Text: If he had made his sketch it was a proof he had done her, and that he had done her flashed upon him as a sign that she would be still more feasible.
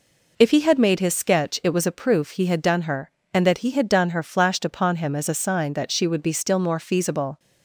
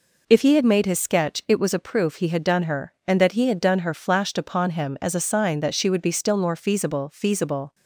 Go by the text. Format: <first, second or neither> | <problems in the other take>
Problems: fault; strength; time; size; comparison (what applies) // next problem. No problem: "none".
first | says "feasible" twice; at 7.1 s